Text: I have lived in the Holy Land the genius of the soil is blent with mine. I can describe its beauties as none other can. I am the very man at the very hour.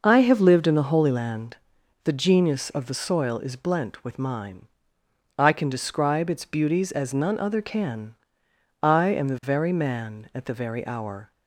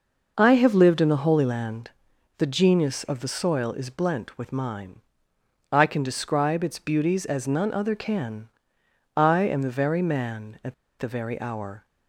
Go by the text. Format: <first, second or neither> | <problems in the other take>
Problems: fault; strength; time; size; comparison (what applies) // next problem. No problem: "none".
first | pauses between "Land" and "the"; noticeable; at 1.9 s; 0.48 s long; noticeable in the first // pauses between "at" and "the"; slight; at 10.7 s; 0.24 s long